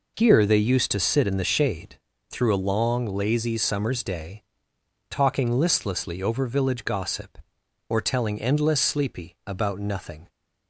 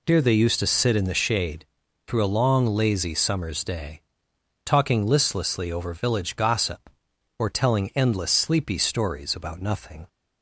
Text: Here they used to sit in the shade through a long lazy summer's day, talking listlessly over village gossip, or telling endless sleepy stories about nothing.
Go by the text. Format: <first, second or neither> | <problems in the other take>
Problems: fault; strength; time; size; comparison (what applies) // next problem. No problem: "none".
second | pauses between "shade" and "through"; slight; at 1.9 s; 0.32 s long; also in the second // skips "stories"; at 9.3 s